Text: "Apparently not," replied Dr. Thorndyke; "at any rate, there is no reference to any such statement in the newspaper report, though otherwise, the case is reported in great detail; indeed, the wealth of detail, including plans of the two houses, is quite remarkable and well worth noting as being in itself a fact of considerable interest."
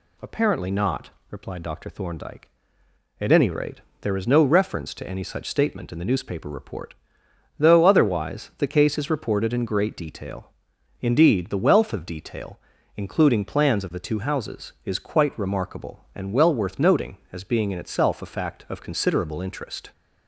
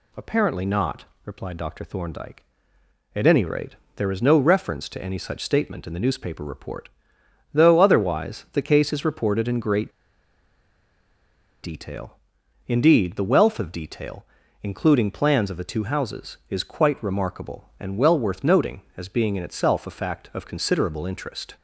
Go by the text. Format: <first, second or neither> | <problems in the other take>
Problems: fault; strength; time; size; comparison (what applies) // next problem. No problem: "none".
first | pauses between "great" and "detail"; strong; at 9.9 s; 1.7 s long